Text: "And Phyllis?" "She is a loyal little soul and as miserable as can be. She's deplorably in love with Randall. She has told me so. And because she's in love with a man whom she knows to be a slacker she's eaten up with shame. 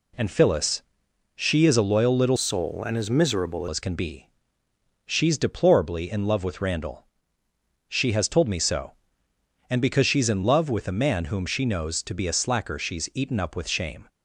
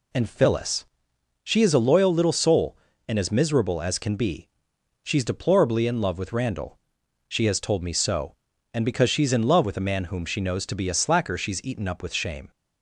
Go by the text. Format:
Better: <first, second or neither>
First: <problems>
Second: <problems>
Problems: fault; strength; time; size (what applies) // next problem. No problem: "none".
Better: second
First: changes voice from "soul" to "miserable"; from 2.3 to 3.6 s; 1.3 s long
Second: none